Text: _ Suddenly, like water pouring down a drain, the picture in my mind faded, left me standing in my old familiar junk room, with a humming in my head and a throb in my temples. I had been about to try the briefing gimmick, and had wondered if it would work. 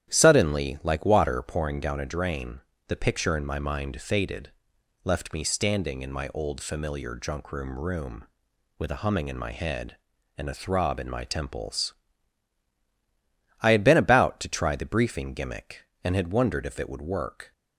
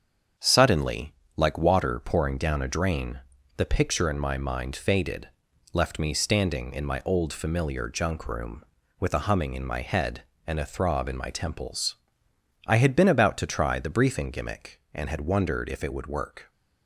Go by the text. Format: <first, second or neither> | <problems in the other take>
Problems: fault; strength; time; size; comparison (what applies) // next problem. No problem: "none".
second | starts louder than the rest; strong; until 1.1 s; 11 dB; strong in the second // says "room" twice; at 7.7 s